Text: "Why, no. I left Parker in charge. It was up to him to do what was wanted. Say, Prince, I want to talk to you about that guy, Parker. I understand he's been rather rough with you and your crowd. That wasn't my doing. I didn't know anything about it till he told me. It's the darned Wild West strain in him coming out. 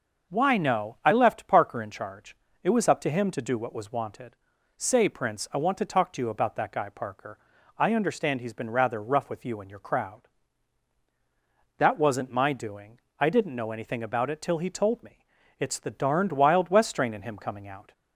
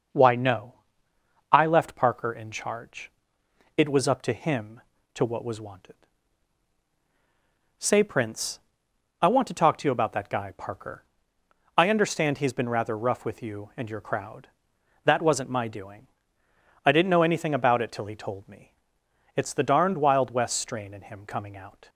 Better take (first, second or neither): first